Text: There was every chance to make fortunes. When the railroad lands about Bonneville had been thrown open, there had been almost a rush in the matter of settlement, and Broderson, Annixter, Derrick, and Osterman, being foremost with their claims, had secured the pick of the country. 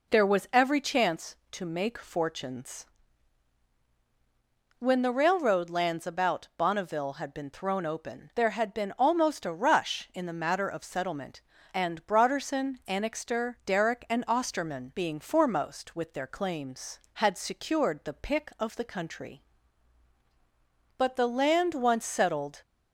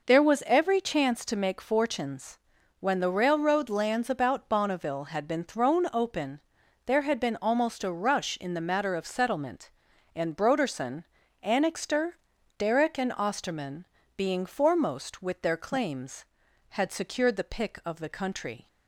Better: second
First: goes on to say "But the land once settled"; from 20.9 s on; 1.6 s long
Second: none

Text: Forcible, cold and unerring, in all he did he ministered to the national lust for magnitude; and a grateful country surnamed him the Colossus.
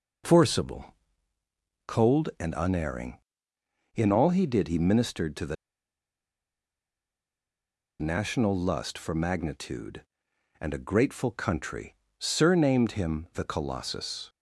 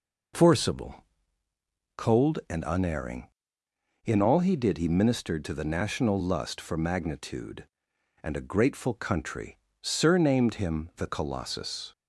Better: second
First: pauses between "the" and "national"; strong; at 5.5 s; 2.4 s long // pauses between "country" and "surnamed"; slight; at 11.9 s; 0.24 s long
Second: pauses between "country" and "surnamed"; slight; at 9.5 s; 0.24 s long

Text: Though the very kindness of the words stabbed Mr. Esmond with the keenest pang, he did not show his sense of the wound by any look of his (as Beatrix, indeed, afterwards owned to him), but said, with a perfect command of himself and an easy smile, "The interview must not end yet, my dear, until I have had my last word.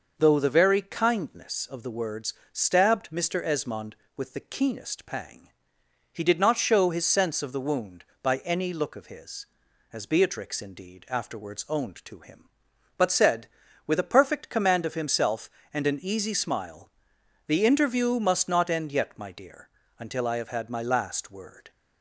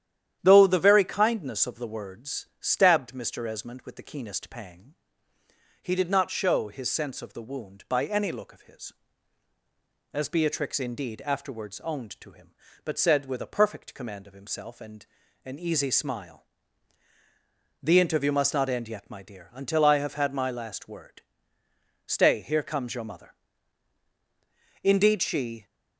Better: first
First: pauses between "words" and "stabbed"; slight; at 2.3 s; 0.18 s long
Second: starts louder than the rest; strong; until 1.4 s; 10.5 dB // pauses between "words" and "stabbed"; slight; at 2.4 s; 0.16 s long // pauses between "and" and "an"; at 15.0 s; 0.38 s long // goes on to say "Stay here comes your mother indeed she"; strong; from 22.0 s on; 3.5 s long

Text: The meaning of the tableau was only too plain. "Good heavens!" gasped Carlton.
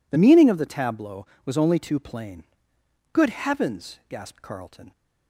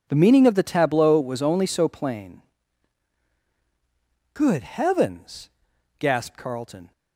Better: first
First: none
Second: says "so" for "too"; at 1.6 s

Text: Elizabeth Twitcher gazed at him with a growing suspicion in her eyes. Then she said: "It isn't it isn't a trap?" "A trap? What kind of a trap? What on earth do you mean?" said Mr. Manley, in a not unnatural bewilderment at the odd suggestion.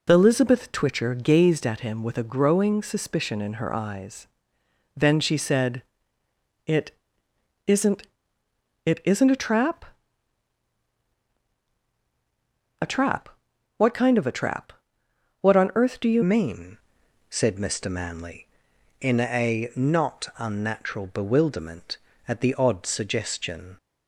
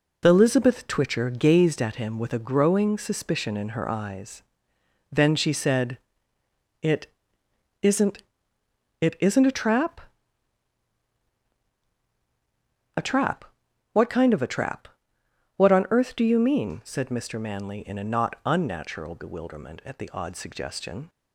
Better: second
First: pauses between "It" and "isn't"; noticeable; at 6.9 s; 0.74 s long // pauses between "isn't" and "it"; noticeable; at 8.0 s; 0.80 s long // changes voice at "mean"; from 16.2 s on; 7.5 s long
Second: pauses between "It" and "isn't"; noticeable; at 7.0 s; 0.74 s long // pauses between "isn't" and "it"; noticeable; at 8.2 s; 0.80 s long

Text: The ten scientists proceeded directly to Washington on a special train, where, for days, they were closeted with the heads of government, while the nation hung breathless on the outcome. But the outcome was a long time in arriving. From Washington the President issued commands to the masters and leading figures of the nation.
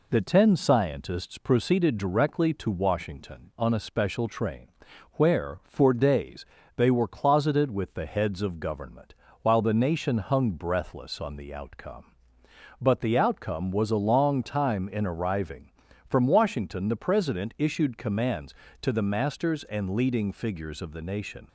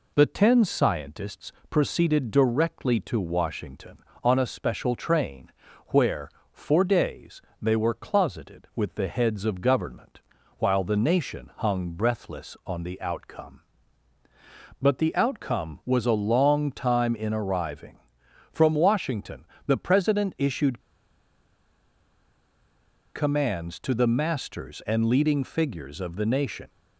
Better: first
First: none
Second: pauses between "scientists" and "proceeded"; slight; at 1.5 s; 0.20 s long // pauses between "Washington" and "the"; slight; at 19.4 s; 0.20 s long // pauses between "issued" and "commands"; strong; at 20.7 s; 2.3 s long

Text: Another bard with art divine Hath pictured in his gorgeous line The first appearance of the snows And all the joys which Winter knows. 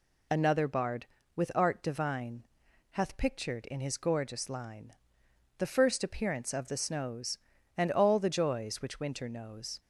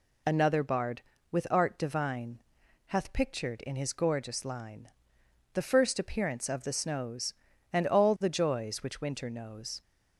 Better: neither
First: pauses between "divine" and "Hath"; noticeable; at 2.4 s; 0.46 s long // pauses between "line" and "The"; noticeable; at 4.9 s; 0.64 s long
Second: pauses between "divine" and "Hath"; noticeable; at 2.4 s; 0.46 s long // pauses between "line" and "The"; noticeable; at 4.8 s; 0.64 s long

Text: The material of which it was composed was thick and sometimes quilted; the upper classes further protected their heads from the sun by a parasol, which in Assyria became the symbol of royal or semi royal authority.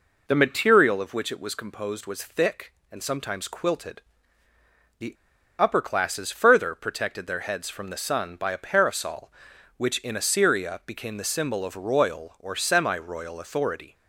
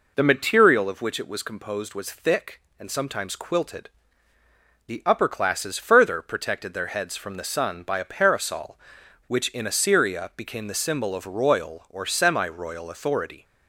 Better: second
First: pauses between "the" and "upper"; at 5.1 s; 0.45 s long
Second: none

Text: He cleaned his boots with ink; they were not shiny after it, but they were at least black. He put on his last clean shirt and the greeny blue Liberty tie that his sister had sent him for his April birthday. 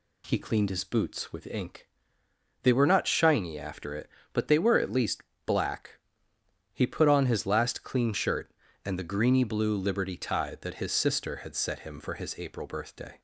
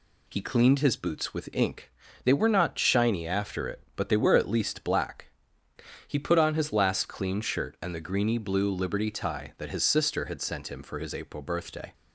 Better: second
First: pauses between "least" and "black"; slight; at 5.2 s; 0.24 s long // says "set" for "sent"; at 11.5 s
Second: none

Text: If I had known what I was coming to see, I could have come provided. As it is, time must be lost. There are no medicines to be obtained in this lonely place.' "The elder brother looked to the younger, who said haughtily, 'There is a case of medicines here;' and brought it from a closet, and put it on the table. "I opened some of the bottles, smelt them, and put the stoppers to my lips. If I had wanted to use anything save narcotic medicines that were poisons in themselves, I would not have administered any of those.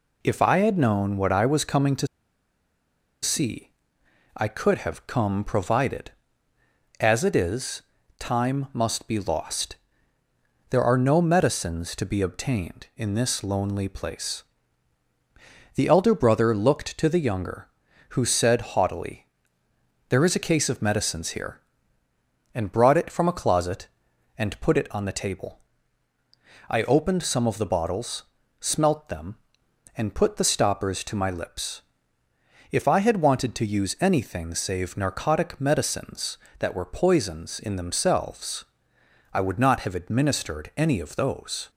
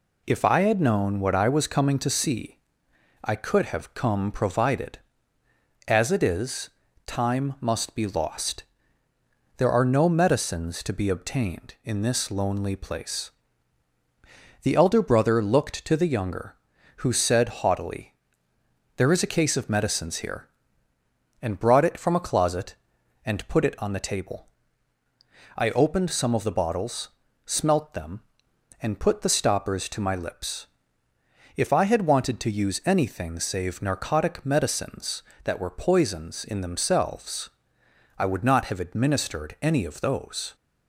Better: second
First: pauses between "to" and "see"; at 2.0 s; 1.1 s long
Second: none

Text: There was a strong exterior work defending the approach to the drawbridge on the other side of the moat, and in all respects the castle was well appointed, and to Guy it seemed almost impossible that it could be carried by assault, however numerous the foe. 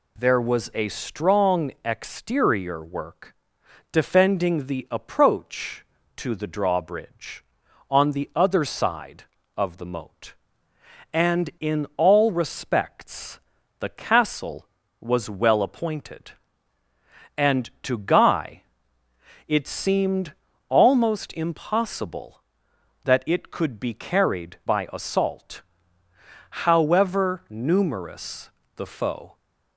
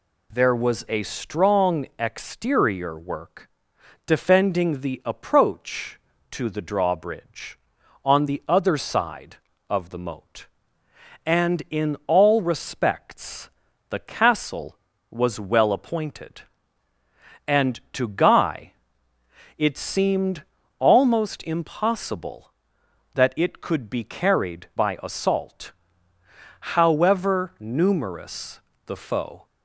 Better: neither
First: pauses between "work" and "defending"; noticeable; at 3.3 s; 0.56 s long // pauses between "respects" and "the"; at 13.3 s; 0.40 s long // pauses between "Guy" and "it"; noticeable; at 18.6 s; 0.84 s long // pauses between "seemed" and "almost"; slight; at 20.3 s; 0.34 s long // pauses between "numerous" and "the"; slight; at 28.4 s; 0.26 s long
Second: pauses between "work" and "defending"; noticeable; at 3.4 s; 0.56 s long // pauses between "respects" and "the"; at 13.4 s; 0.40 s long // pauses between "Guy" and "it"; noticeable; at 18.7 s; 0.84 s long // pauses between "seemed" and "almost"; slight; at 20.4 s; 0.34 s long // pauses between "numerous" and "the"; slight; at 28.5 s; 0.26 s long

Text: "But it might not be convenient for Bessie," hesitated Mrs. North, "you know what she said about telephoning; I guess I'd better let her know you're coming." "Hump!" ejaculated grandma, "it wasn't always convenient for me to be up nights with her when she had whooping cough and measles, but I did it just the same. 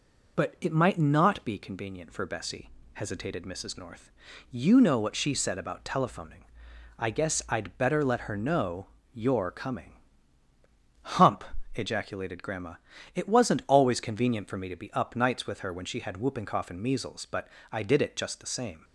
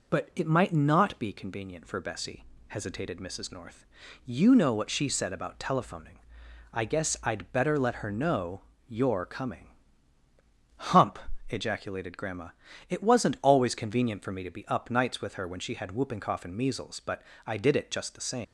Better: first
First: pauses between "know" and "you're"; slight; at 8.8 s; 0.26 s long // pauses between "but" and "I"; slight; at 17.4 s; 0.24 s long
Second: pauses between "know" and "you're"; slight; at 8.6 s; 0.26 s long // pauses between "but" and "I"; slight; at 17.2 s; 0.24 s long // leaves "same" unfinished; at 18.4 s; 135 ms

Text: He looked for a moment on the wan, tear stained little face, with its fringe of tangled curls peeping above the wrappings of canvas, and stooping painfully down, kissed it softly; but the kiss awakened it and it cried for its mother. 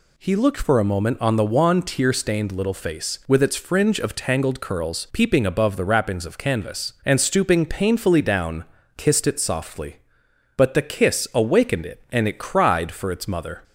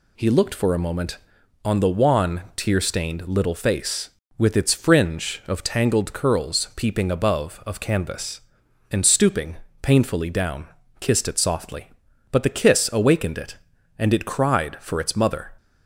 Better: first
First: none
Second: skips "the wrappings"; at 7.6 s // pauses between "stooping" and "painfully"; slight; at 9.5 s; 0.26 s long

